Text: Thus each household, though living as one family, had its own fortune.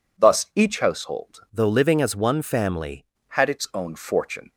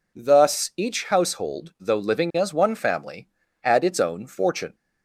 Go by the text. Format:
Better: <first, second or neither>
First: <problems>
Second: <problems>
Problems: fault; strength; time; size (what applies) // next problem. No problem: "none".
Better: second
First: changes voice from "though" to "family"; from 1.5 to 3.0 s; 1.5 s long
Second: none